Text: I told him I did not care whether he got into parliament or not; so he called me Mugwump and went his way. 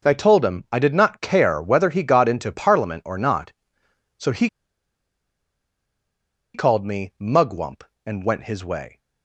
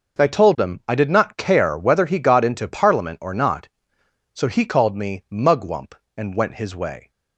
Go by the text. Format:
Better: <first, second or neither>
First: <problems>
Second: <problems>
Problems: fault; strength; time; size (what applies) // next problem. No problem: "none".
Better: second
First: pauses between "he" and "called"; strong; at 4.4 s; 2.0 s long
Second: none